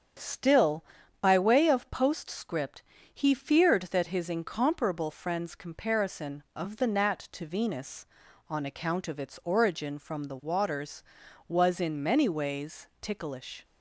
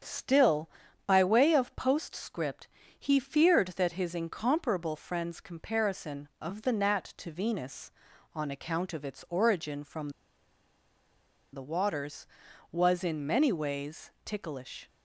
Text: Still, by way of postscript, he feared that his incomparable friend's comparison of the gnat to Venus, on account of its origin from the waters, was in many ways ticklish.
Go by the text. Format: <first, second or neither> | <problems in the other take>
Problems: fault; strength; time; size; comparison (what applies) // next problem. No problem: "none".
first | starts louder than the rest; strong; until 1.4 s; 7.5 dB; strong in the first // pauses between "from" and "the"; strong; at 10.0 s; 1.4 s long